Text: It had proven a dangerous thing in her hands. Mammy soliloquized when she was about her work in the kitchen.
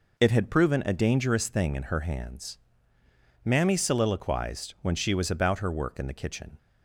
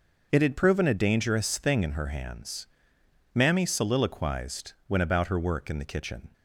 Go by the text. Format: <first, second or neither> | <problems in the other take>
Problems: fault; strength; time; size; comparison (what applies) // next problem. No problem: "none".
first | pauses between "soliloquized" and "when"; slight; at 4.7 s; 0.16 s long // skips "she was"; at 4.9 s